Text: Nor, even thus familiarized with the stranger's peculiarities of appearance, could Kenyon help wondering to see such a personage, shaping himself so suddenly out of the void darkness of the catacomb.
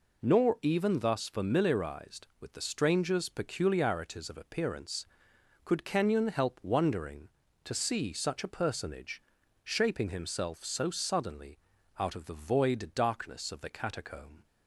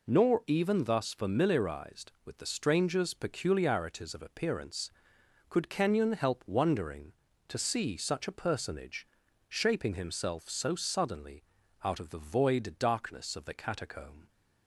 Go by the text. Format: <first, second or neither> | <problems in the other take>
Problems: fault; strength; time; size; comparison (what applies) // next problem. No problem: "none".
neither | pauses between "suddenly" and "out"; the same in both